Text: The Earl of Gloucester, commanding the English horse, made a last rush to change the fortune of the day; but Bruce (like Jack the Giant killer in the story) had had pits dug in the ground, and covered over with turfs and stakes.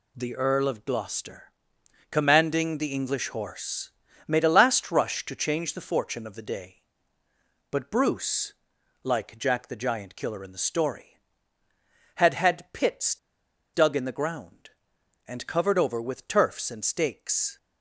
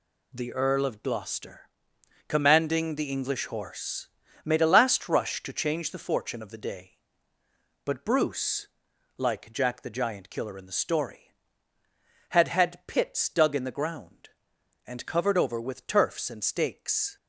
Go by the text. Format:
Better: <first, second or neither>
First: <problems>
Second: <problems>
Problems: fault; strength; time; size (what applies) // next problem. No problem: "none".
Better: second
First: pauses between "pits" and "dug"; noticeable; at 13.1 s; 0.61 s long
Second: none